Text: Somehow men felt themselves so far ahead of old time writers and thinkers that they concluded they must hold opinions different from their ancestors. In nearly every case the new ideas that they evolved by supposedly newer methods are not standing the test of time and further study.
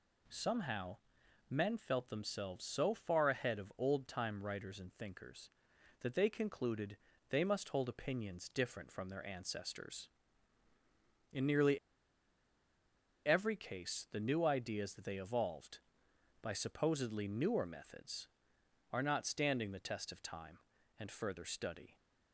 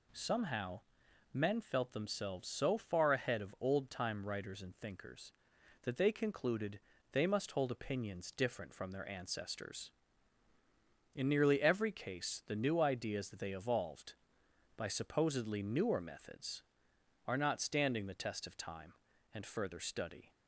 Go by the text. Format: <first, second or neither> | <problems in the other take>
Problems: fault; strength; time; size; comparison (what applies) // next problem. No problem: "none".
second | pauses between "Somehow" and "men"; noticeable; at 0.9 s; 0.52 s long; noticeable in the second // pauses between "concluded" and "they"; slight; at 6.9 s; 0.32 s long; slight in the second // pauses between "nearly" and "every"; strong; at 11.7 s; 1.4 s long